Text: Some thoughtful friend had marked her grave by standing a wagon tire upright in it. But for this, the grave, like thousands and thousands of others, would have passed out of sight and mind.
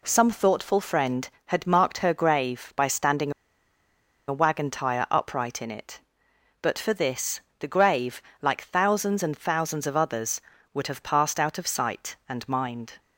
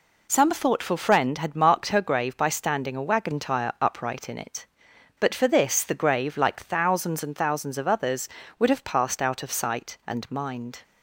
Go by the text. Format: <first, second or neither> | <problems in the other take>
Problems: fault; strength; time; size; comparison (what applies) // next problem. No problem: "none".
second | pauses between "standing" and "a"; noticeable; at 3.3 s; 0.96 s long